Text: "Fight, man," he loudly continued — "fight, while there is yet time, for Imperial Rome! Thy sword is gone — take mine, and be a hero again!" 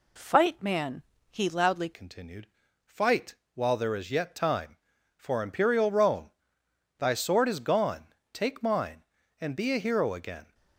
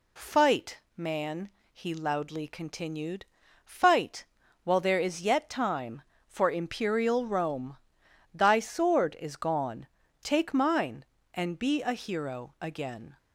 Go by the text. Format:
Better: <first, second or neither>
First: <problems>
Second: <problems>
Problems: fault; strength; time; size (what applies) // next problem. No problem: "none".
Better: second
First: changes voice at "continued"; from 1.9 s on; 8.6 s long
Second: none